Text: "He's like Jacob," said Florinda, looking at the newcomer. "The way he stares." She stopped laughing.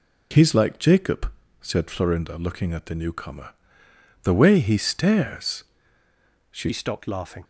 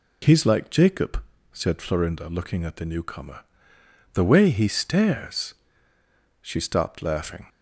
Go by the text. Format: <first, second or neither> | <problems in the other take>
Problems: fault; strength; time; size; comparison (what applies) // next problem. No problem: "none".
second | changes voice at "stopped"; from 6.7 s on; 0.7 s long